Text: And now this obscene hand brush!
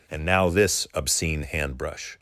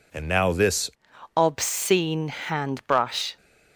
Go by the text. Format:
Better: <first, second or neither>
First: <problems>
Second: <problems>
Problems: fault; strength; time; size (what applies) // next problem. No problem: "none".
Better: first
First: none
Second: changes voice at "obscene"; from 1.3 s on; 2.0 s long